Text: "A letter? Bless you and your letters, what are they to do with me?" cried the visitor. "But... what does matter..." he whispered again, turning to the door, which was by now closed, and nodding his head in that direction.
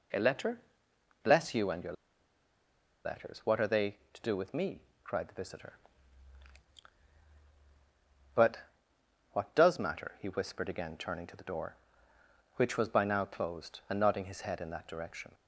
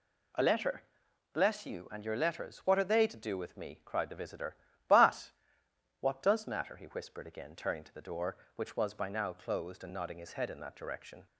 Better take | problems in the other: second | pauses between "your" and "letters"; at 1.9 s; 1.1 s long

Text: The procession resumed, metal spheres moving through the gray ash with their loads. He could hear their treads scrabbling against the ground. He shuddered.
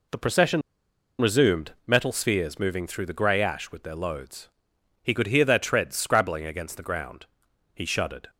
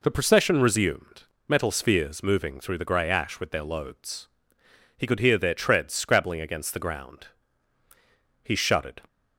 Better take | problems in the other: second | pauses between "procession" and "resumed"; noticeable; at 0.6 s; 0.59 s long

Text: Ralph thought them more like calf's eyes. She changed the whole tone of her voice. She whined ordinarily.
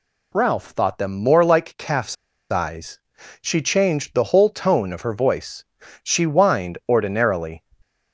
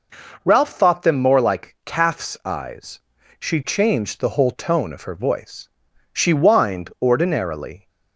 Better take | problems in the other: second | pauses between "calf's" and "eyes"; at 2.1 s; 0.36 s long

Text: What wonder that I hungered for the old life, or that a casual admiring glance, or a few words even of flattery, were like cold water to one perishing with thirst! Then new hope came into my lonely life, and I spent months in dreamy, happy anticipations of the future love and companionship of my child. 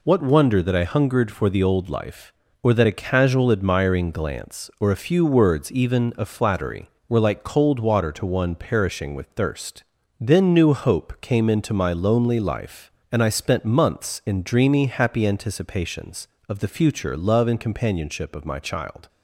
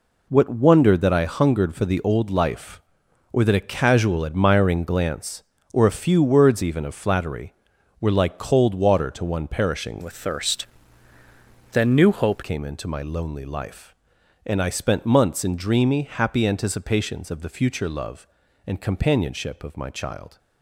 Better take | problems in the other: first | changes voice from "with" to "hope"; from 10.0 to 12.4 s; 2.4 s long

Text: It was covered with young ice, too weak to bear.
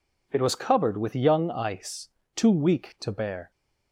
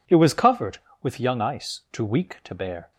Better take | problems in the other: neither | none

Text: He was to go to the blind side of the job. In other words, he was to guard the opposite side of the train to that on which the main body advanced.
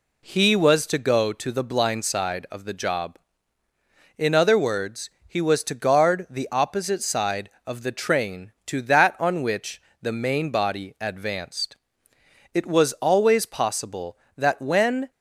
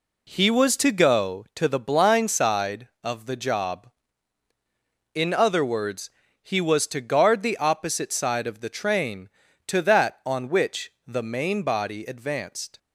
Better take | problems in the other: second | pauses between "which" and "the"; slight; at 9.8 s; 0.18 s long // goes on to say "It was always possible that when"; strong; from 12.5 s on; 2.5 s long

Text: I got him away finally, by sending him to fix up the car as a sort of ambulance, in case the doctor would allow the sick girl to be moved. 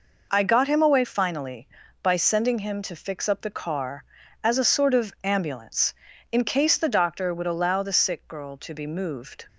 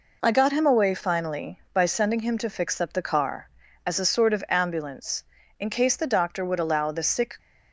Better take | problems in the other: first | stops before "girl to be moved"; at 7.3 s

